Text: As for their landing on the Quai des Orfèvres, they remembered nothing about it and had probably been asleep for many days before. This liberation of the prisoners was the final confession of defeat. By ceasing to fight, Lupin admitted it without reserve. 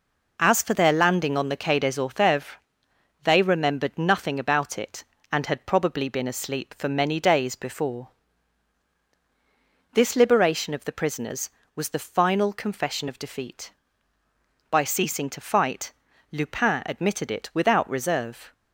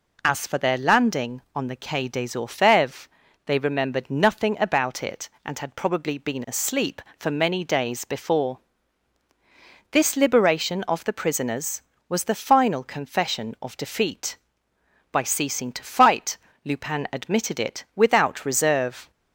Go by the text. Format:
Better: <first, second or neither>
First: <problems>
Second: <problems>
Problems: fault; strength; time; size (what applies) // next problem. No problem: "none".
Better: neither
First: none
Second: none